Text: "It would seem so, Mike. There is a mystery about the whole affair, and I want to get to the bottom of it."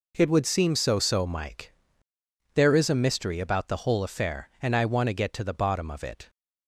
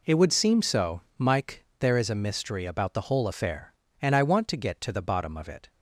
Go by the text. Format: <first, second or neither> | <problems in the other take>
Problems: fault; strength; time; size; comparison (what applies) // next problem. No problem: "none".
second | says "so" twice; at 0.9 s